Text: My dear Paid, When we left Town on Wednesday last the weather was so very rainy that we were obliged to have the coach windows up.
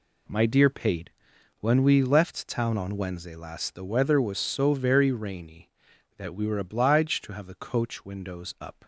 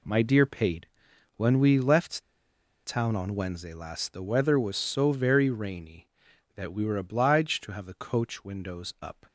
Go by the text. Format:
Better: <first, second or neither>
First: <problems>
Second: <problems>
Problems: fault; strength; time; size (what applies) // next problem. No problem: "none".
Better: first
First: none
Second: pauses between "left" and "Town"; noticeable; at 2.2 s; 0.64 s long